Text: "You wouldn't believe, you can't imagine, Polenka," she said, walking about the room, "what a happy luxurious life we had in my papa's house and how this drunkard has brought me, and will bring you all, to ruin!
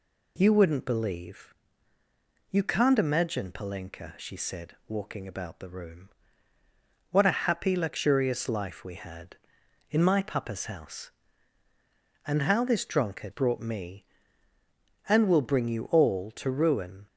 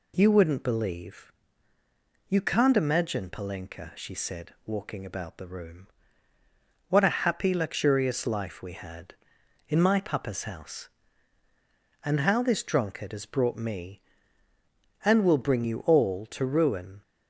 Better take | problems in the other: second | skips "has"; at 13.3 s

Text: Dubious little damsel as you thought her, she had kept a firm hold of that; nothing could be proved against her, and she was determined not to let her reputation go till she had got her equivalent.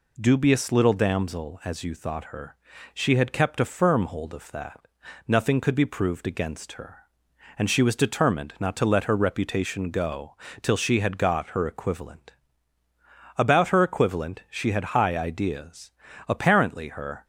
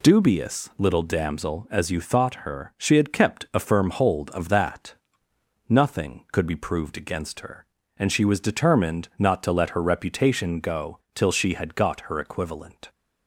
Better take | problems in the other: second | pauses between "go" and "till"; slight; at 10.3 s; 0.26 s long; slight in the second // goes on to say "About her equivalent she had high ideas Apparently her"; strong; from 13.3 s on; 3.8 s long

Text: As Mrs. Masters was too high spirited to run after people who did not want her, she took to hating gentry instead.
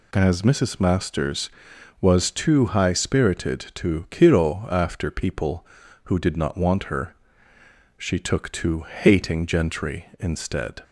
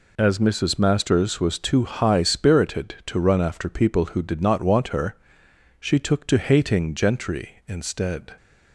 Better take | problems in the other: second | says "kiro" for "run"; at 4.0 s

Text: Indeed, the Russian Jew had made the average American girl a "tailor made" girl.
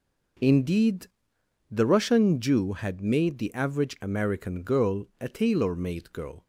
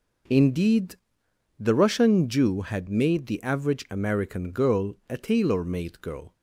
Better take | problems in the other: neither | none

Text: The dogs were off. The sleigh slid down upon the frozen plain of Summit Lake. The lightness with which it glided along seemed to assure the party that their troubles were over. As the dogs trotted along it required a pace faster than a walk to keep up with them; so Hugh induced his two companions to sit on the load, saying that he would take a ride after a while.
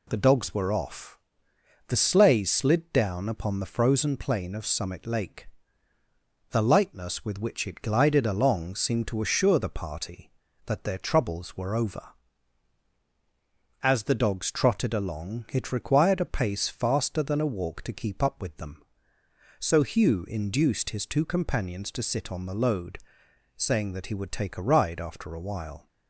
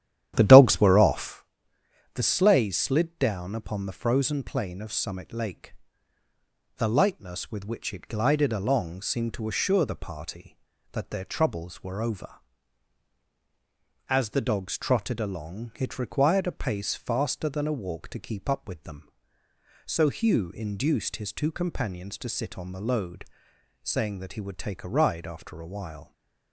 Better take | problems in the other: first | starts louder than the rest; strong; until 1.4 s; 11 dB

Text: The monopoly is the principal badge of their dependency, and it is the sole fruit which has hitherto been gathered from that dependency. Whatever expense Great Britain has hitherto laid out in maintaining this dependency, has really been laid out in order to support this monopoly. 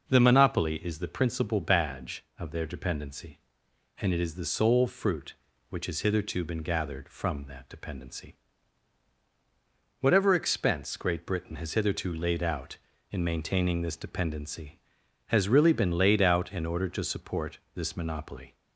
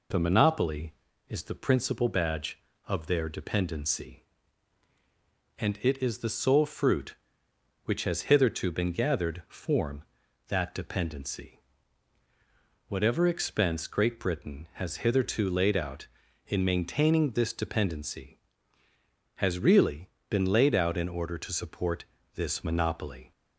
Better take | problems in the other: first | says "form" for "from"; at 9.4 s // pauses between "really" and "been"; slight; at 20.0 s; 0.18 s long // pauses between "support" and "this"; slight; at 22.0 s; 0.32 s long; slight in the first

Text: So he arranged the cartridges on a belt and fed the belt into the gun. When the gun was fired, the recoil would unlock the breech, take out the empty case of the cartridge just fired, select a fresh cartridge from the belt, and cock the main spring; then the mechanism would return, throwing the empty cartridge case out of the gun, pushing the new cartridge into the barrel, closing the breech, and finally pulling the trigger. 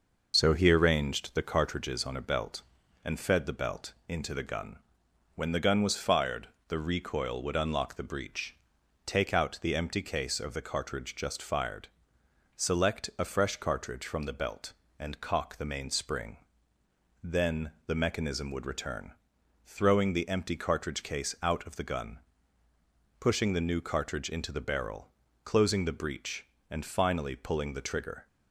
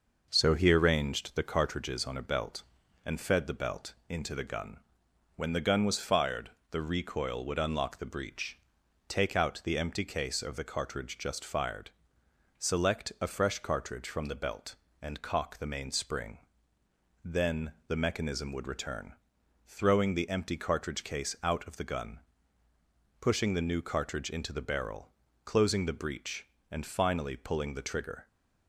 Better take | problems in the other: second | loses the start of "So"; at 0.3 s; 60 ms // pauses between "belt" and "into"; slight; at 3.9 s; 0.16 s long; slight in the second // pauses between "then" and "the"; slight; at 17.7 s; 0.16 s long; slight in the second

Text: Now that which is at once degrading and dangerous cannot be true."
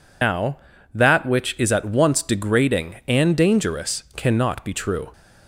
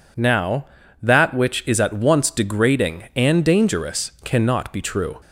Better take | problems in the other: second | loses the start of "Now"; at 0.2 s; 130 ms

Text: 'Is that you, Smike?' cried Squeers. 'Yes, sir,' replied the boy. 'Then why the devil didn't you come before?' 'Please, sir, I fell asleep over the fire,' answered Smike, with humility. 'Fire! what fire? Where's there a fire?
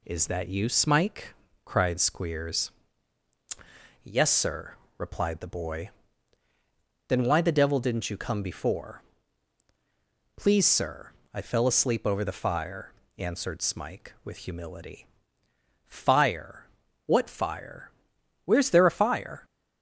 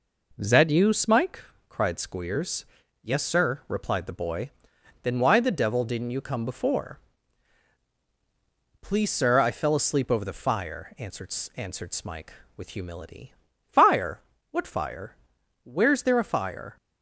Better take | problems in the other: first | says "answered" twice; at 11.5 s

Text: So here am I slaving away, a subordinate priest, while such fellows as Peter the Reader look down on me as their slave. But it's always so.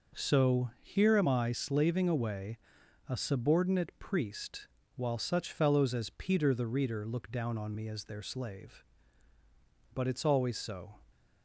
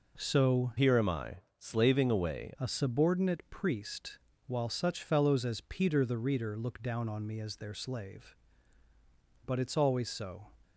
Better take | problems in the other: first | changes voice from "here" to "away"; from 0.7 to 2.5 s; 1.8 s long // pauses between "I" and "slaving"; slight; at 1.3 s; 0.20 s long

